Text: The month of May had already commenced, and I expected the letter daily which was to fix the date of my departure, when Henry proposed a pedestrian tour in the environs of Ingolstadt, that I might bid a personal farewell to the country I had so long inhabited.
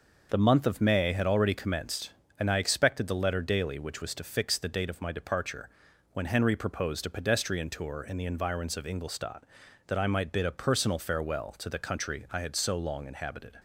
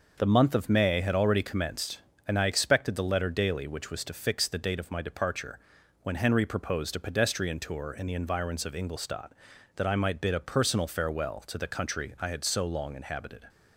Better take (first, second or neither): neither